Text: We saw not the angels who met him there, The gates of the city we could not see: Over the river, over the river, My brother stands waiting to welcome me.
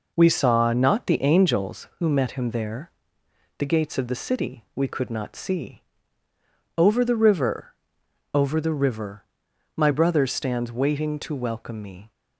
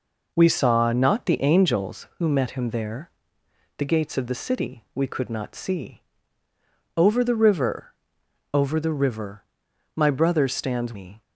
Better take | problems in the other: first | skips "waiting to welcome"; at 10.9 s

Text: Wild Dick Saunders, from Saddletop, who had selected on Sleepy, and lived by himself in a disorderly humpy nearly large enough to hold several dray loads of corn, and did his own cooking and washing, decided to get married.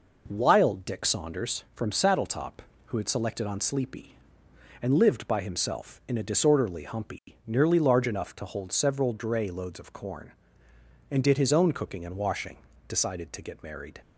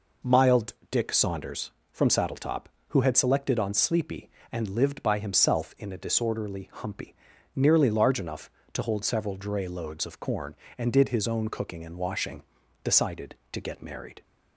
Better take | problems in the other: first | says "Mild" for "Wild"; at 0.2 s // pauses between "humpy" and "nearly"; at 7.1 s; 0.40 s long; slight in the first

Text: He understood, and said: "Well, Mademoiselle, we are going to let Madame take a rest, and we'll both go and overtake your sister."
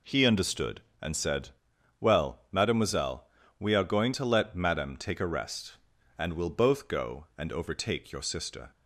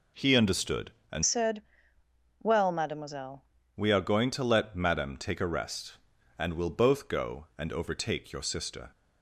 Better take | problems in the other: first | changes voice from "said" to "Mademoiselle"; from 1.2 to 3.4 s; 2.2 s long

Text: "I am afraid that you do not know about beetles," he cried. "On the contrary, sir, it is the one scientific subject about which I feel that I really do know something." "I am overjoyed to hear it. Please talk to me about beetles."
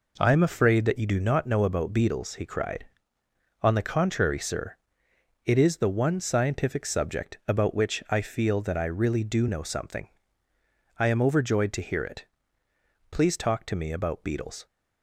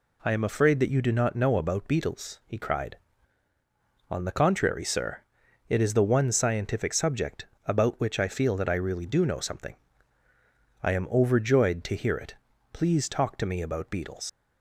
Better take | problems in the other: first | pauses between "subject" and "about"; slight; at 7.4 s; 0.20 s long // leaves "beetles" unfinished; at 14.2 s; 100 ms

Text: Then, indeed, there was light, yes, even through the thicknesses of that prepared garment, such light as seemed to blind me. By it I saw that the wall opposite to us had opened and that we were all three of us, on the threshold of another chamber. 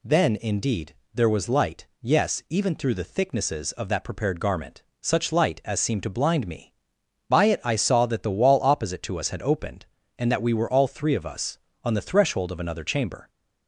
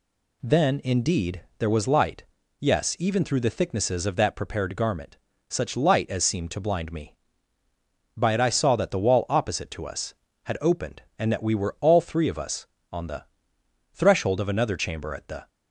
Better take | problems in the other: first | pauses between "the" and "threshold"; noticeable; at 13.2 s; 0.68 s long // goes on to say "At the"; slight; from 15.1 s on; 0.34 s long

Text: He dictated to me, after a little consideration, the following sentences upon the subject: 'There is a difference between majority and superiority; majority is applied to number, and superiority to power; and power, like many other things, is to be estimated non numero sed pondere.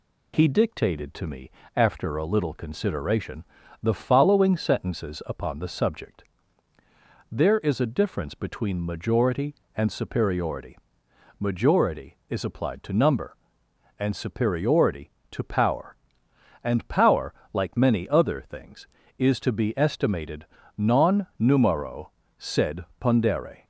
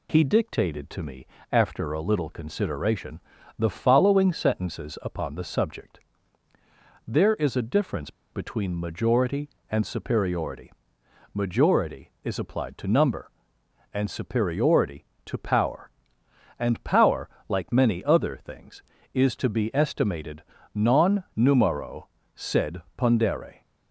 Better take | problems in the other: first | pauses between "difference" and "between"; slight; at 8.1 s; 0.21 s long // pauses between "estimated" and "non"; slight; at 20.4 s; 0.32 s long; slight in the first // pauses between "numero" and "sed"; slight; at 22.0 s; 0.28 s long; slight in the first // pauses between "sed" and "pondere"; slight; at 22.8 s; 0.16 s long; slight in the first

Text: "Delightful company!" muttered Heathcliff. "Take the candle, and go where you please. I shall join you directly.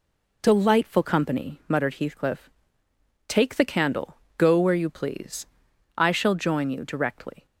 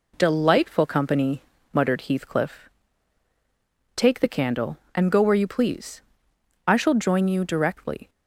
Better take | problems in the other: second | skips "and"; at 4.2 s

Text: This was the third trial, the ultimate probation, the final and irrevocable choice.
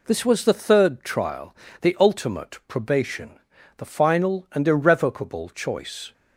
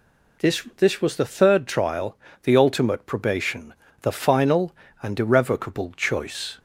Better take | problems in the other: first | says "This" twice; at 0.7 s

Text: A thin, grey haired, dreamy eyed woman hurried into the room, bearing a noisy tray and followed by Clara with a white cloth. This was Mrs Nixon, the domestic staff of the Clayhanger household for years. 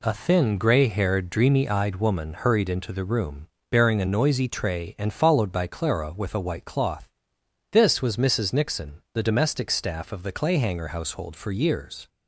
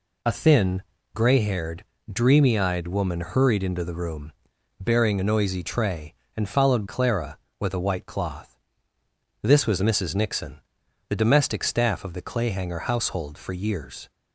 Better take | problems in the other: first | skips "by"; at 6.8 s

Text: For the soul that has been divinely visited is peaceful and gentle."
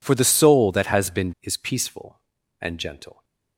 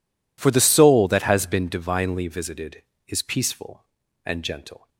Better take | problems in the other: second | skips "divinely visited"; at 1.3 s

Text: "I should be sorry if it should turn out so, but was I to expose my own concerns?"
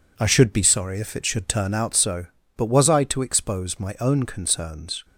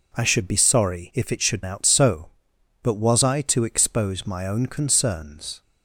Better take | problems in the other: first | skips "turn"; at 1.6 s

